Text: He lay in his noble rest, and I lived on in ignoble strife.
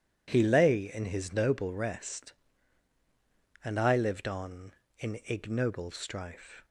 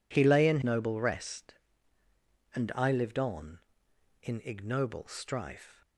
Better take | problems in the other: first | skips "his"; at 0.6 s

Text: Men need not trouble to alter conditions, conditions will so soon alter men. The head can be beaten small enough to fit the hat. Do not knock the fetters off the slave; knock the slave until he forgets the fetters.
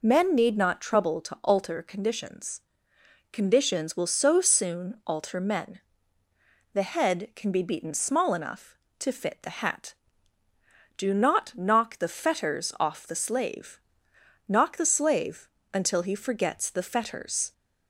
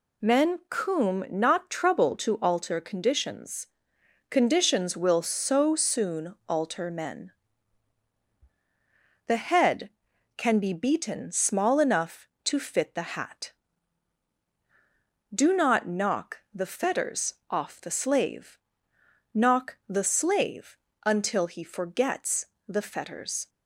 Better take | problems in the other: first | says "coom" for "need"; at 0.6 s // pauses between "soon" and "alter"; slight; at 6.3 s; 0.16 s long // pauses between "fetters" and "off"; slight; at 17.3 s; 0.16 s long // pauses between "slave" and "until"; slight; at 20.7 s; 0.28 s long; slight in the first // pauses between "forgets" and "the"; slight; at 22.4 s; 0.20 s long

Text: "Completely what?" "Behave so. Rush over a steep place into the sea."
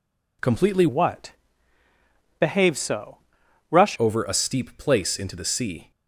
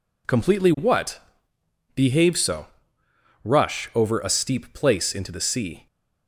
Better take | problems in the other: second | changes voice from "what" to "Rush"; from 0.8 to 3.9 s; 3.1 s long

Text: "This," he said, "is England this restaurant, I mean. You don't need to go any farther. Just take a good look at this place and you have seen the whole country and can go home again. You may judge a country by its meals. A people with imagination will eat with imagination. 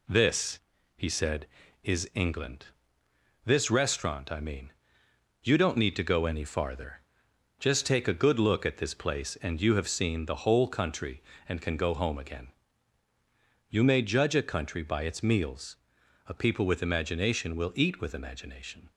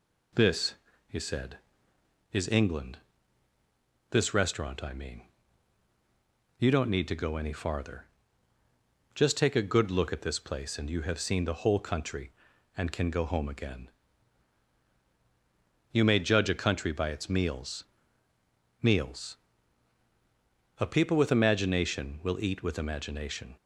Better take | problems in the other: first | pauses between "England" and "this"; at 2.9 s; 1.1 s long; noticeable in the first // says "meals" twice; at 18.8 s

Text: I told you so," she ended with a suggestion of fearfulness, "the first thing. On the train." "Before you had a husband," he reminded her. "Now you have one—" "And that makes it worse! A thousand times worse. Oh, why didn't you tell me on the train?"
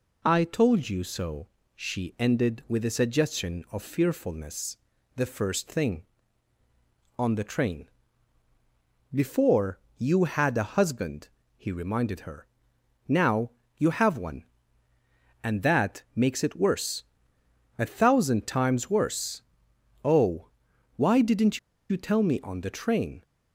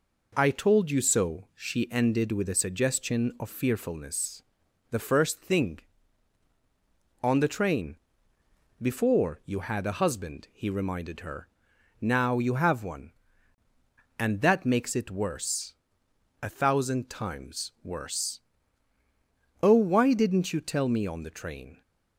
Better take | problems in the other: second | pauses between "Before" and "you"; slight; at 9.7 s; 0.18 s long // pauses between "Now" and "you"; slight; at 13.5 s; 0.24 s long // pauses between "didn't" and "you"; slight; at 21.5 s; 0.31 s long

